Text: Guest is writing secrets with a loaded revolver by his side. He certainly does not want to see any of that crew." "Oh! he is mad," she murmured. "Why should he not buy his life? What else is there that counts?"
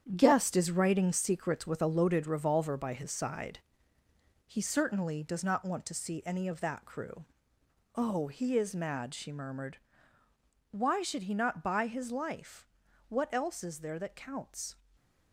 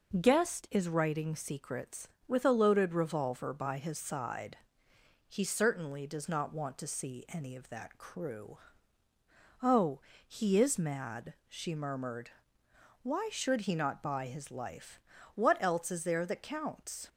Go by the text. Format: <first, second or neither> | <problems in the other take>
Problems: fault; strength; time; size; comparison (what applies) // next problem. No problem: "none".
second | gets quieter; strong; throughout; 8.5 dB // stays silent after the last word; slight; from 14.7 s on; 0.6 s long